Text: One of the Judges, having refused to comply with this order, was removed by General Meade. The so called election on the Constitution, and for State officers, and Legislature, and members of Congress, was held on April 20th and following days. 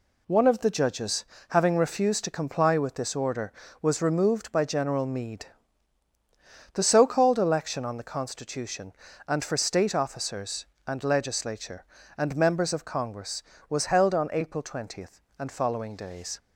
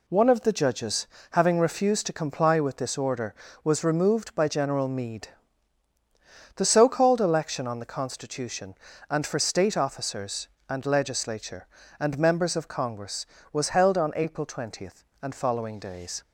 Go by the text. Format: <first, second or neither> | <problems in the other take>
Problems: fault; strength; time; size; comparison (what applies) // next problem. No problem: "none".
neither | none